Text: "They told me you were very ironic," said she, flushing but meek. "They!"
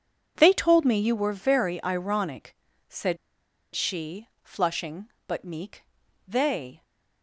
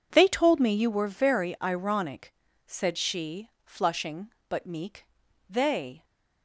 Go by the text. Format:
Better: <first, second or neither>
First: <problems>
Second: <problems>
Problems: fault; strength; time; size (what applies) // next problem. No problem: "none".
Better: second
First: pauses between "said" and "she"; noticeable; at 3.1 s; 0.57 s long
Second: none